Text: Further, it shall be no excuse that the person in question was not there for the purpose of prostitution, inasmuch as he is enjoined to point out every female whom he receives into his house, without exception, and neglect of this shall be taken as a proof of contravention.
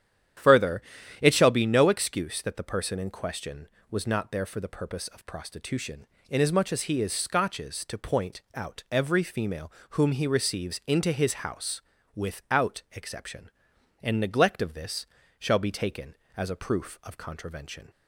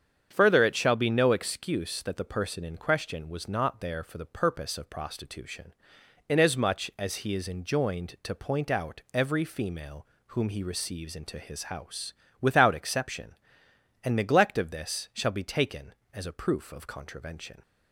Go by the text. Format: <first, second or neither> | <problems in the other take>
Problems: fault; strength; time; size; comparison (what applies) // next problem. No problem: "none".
second | starts louder than the rest; strong; until 1.8 s; 10 dB; strong in the second // says "scotches" for "enjoined"; at 7.1 s // pauses between "female" and "whom"; slight; at 9.7 s; 0.18 s long; slight in the second // pauses between "this" and "shall"; slight; at 15.0 s; 0.34 s long